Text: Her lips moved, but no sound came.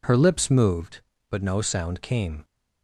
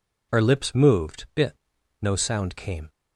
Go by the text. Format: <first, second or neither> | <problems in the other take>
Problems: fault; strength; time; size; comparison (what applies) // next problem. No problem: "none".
first | says "bit" for "but"; at 1.3 s